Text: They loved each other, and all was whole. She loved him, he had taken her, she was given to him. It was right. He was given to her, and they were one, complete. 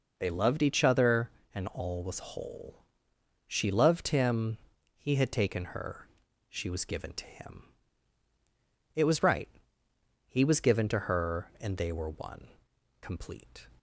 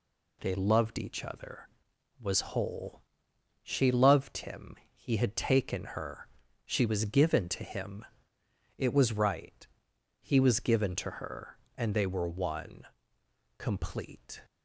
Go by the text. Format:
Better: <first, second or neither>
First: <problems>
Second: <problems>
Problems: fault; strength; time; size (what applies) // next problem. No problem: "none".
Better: first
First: none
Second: skips "and all"; at 1.9 s